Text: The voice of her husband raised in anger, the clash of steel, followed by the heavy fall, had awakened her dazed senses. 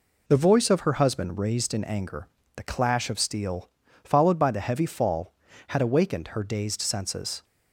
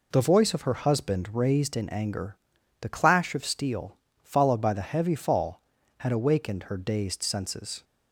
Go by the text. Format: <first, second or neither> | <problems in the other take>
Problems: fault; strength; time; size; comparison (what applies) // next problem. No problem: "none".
neither | none